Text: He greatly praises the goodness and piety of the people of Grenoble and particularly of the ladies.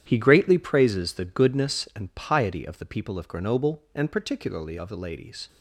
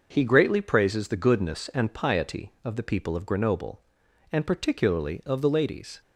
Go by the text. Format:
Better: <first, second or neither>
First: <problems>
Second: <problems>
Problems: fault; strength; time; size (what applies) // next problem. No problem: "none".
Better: second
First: gets quieter; strong; throughout; 10.5 dB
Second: none